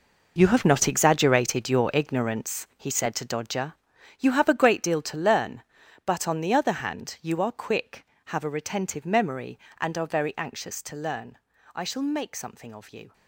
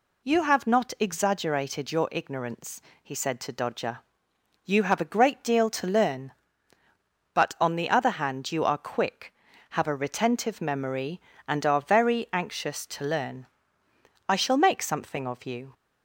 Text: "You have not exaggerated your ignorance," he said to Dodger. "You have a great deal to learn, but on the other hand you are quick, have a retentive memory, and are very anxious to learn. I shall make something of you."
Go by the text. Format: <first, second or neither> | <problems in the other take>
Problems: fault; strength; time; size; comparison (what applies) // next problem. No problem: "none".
second | gets quieter; strong; throughout; 13 dB